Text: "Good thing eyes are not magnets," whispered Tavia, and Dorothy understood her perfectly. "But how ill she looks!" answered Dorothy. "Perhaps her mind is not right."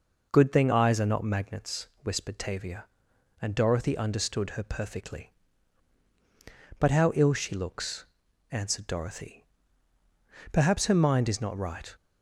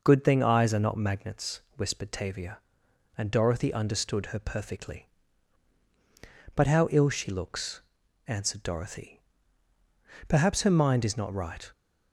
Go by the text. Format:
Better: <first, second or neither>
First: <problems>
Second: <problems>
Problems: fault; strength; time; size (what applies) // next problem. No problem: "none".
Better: neither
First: none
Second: none